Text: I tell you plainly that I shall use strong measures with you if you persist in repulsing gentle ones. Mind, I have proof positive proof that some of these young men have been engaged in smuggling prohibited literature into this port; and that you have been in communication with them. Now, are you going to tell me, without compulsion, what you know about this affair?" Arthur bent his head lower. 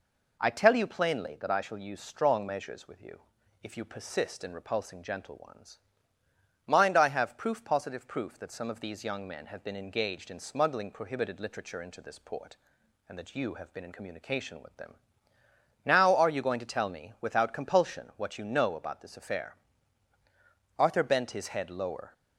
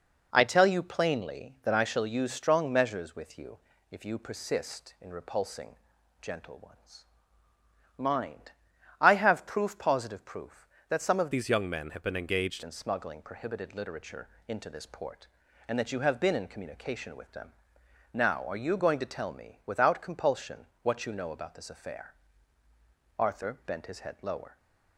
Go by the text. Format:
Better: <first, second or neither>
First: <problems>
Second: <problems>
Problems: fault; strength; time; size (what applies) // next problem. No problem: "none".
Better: first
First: pauses between "you" and "if"; at 3.1 s; 0.42 s long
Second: pauses between "you" and "if"; slight; at 3.5 s; 0.32 s long // pauses between "repulsing" and "gentle"; at 5.7 s; 0.44 s long // changes voice from "these" to "engaged"; from 11.3 to 12.6 s; 1.3 s long // pauses between "literature" and "into"; slight; at 14.2 s; 0.20 s long